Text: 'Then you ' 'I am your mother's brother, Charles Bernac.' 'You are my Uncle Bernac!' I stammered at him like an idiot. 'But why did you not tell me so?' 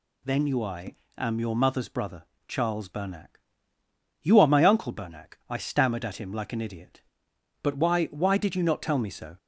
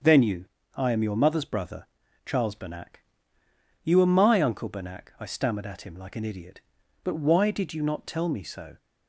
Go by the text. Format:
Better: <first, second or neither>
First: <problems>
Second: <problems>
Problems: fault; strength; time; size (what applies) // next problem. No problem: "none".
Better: second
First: pauses between "I" and "am"; slight; at 0.9 s; 0.22 s long // says "why" twice; at 8.0 s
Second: none